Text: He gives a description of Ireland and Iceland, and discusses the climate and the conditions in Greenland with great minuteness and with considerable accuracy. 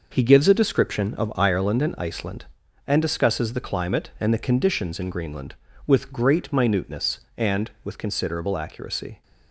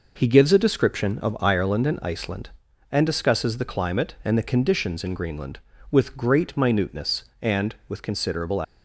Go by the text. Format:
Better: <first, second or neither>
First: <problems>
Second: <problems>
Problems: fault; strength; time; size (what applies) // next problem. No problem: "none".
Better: first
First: none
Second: stops before "accuracy"; at 8.6 s